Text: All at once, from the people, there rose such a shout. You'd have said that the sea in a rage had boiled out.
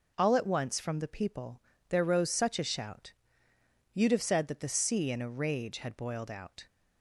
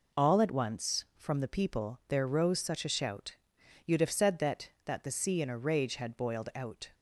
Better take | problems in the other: first | says "that" twice; at 4.8 s

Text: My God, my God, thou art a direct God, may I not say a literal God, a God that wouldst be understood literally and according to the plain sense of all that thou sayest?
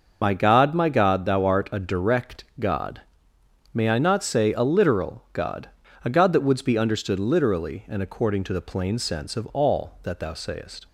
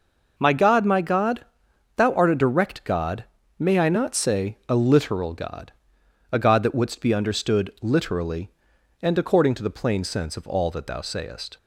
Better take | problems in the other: second | loses the start of "My"; at 0.2 s; 35 ms // starts louder than the rest; noticeable; until 1.2 s; 6 dB

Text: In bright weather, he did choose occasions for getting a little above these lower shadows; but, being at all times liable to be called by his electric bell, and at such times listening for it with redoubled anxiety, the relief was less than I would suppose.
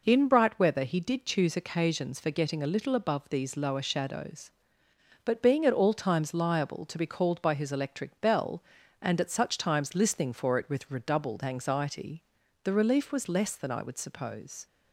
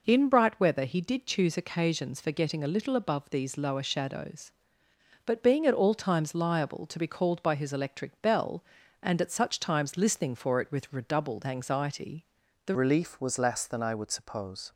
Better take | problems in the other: first | changes voice at "relief"; from 12.7 s on; 2.0 s long

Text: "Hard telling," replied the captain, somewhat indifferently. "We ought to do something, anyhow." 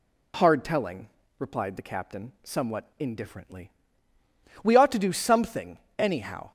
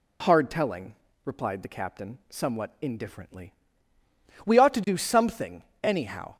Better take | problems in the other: neither | none

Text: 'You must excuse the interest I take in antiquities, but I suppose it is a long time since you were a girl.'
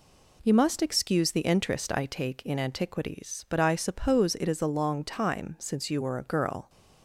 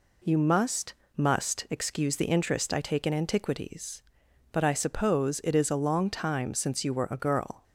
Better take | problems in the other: first | says "must" twice; at 1.1 s

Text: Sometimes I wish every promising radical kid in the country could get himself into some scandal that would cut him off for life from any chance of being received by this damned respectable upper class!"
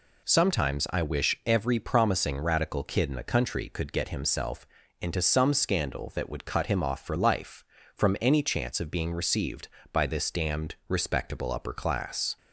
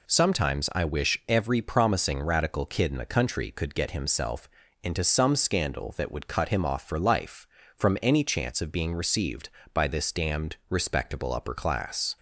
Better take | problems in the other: neither | pauses between "himself" and "into"; slight; the same in both

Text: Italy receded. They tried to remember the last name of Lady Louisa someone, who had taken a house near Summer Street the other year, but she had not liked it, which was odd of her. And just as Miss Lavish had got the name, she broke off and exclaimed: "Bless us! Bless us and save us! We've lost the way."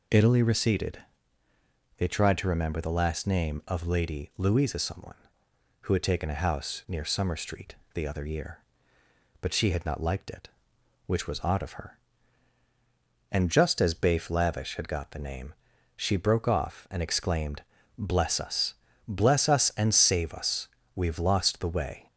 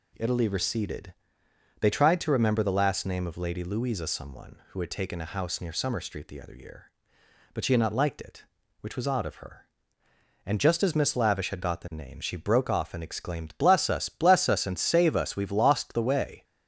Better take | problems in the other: second | pauses between "Street" and "the"; slight; at 7.7 s; 0.20 s long // says "Bafe" for "Miss"; at 13.9 s

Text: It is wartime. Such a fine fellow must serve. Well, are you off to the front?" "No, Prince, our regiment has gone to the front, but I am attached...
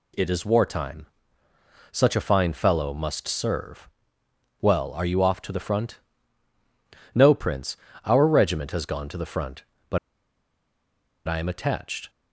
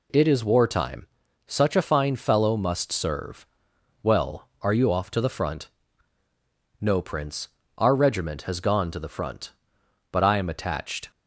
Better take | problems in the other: second | pauses between "but" and "I"; strong; at 9.9 s; 1.2 s long

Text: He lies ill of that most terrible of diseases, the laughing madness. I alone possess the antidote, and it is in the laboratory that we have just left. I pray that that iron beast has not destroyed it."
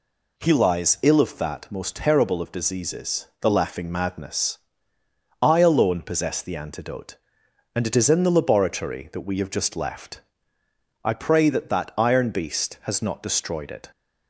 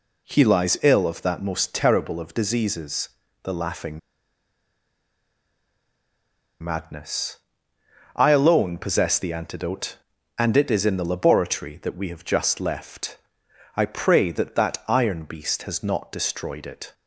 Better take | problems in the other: first | pauses between "laughing" and "madness"; strong; at 3.9 s; 2.6 s long

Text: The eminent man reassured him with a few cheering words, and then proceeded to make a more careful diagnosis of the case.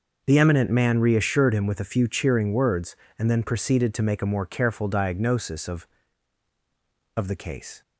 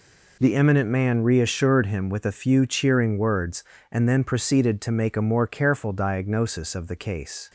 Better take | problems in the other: second | starts louder than the rest; until 1.2 s; 6.5 dB // says "of" twice; at 7.1 s

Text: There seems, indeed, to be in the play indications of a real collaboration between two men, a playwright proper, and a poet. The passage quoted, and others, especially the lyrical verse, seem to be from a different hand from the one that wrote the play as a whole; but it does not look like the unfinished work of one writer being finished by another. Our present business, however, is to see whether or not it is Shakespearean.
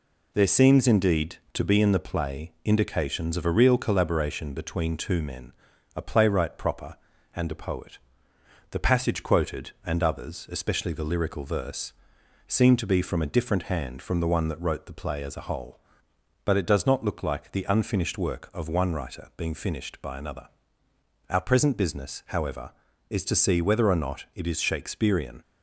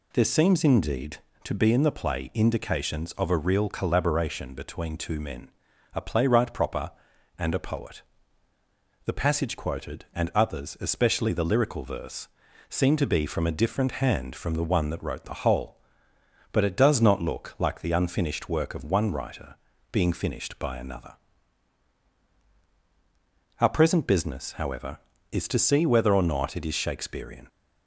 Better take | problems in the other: first | skips "play as a"; at 15.4 s // pauses between "writer" and "being"; at 19.5 s; 0.38 s long

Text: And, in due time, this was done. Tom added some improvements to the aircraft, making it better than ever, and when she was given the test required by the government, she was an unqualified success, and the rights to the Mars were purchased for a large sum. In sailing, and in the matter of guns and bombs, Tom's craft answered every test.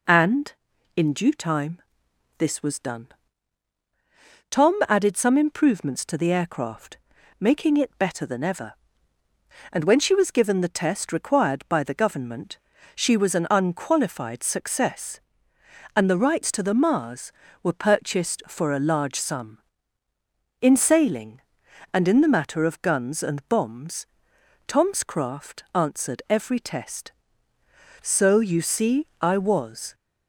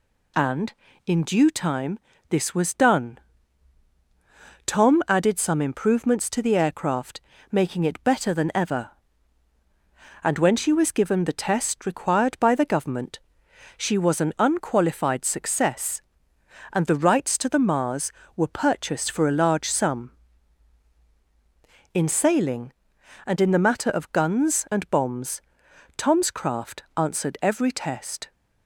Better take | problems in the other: second | goes on to say "So you see I was"; strong; from 28.0 s on; 1.9 s long

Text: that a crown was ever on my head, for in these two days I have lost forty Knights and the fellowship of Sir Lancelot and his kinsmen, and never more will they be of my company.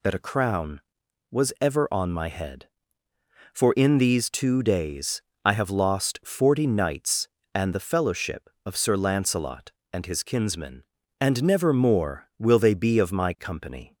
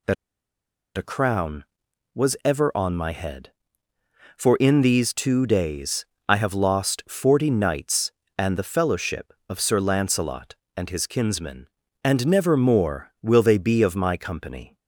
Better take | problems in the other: first | pauses between "that" and "a"; noticeable; at 0.1 s; 0.82 s long // pauses between "days" and "I"; slight; at 6.0 s; 0.22 s long; slight in the first

